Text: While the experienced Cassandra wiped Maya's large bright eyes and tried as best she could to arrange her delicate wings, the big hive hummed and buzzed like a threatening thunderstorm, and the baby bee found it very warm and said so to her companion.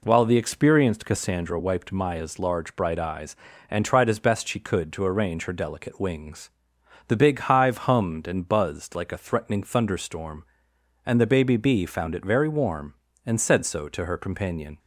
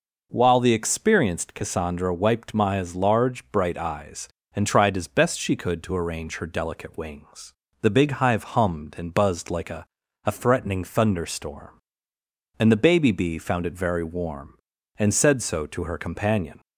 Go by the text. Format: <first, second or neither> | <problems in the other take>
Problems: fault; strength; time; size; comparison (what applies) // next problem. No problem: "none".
first | says "a" twice; at 10.2 s